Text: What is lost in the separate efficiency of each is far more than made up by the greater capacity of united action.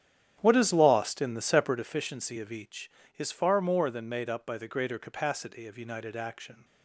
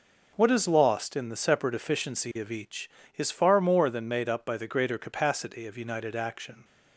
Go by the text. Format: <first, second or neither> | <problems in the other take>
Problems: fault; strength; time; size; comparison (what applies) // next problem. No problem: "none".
second | starts louder than the rest; strong; until 1.8 s; 10 dB